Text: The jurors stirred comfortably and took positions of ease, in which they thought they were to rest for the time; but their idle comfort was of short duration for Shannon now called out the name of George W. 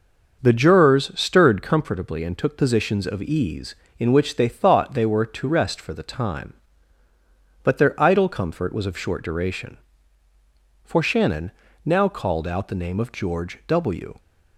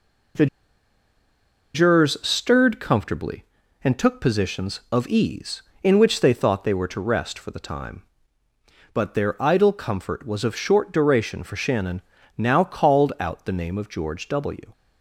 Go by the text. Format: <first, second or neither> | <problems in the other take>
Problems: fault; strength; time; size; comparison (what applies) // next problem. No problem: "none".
first | pauses between "The" and "jurors"; strong; at 0.4 s; 1.2 s long // pauses between "Shannon" and "now"; slight; at 12.0 s; 0.34 s long; slight in the first